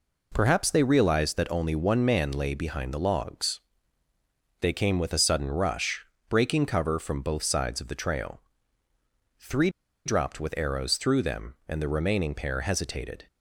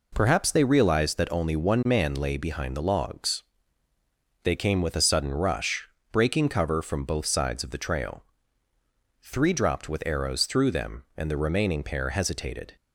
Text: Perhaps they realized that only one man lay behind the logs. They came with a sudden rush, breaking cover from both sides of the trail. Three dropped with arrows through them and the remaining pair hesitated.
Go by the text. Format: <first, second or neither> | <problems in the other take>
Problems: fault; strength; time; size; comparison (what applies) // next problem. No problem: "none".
second | pauses between "Three" and "dropped"; at 9.6 s; 0.36 s long